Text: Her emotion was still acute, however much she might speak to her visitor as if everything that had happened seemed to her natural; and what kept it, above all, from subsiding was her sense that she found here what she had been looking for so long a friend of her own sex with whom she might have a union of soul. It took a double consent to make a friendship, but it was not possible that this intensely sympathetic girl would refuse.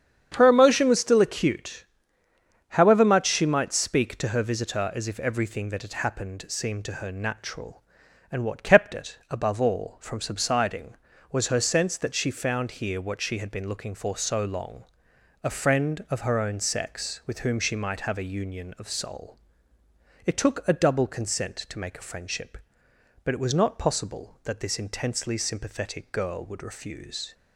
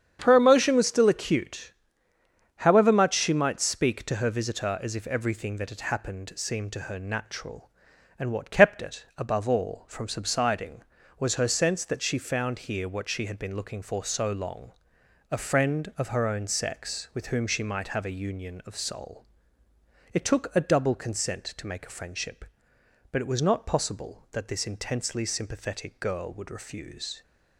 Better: neither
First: starts louder than the rest; strong; until 1.3 s; 8 dB // pauses between "long" and "a"; noticeable; at 14.8 s; 0.58 s long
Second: starts louder than the rest; strong; until 1.2 s; 8 dB // pauses between "long" and "a"; noticeable; at 14.7 s; 0.58 s long

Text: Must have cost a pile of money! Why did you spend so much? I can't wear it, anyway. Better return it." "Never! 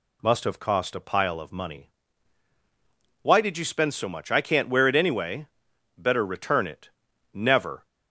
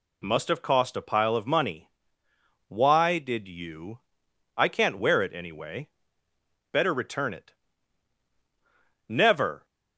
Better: first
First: none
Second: skips "spend so much"; at 4.2 s

